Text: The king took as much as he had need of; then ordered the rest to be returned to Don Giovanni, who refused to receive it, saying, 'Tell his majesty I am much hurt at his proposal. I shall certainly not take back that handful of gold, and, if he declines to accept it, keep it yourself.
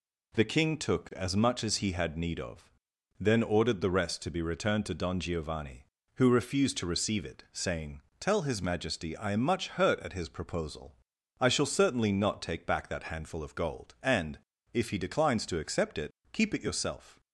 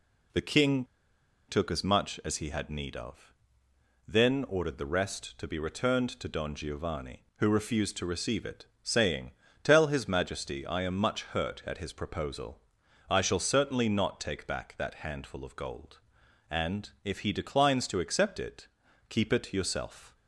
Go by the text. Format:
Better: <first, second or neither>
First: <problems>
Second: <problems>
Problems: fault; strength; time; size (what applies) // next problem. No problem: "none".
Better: first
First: none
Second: pauses between "king" and "took"; noticeable; at 0.8 s; 0.64 s long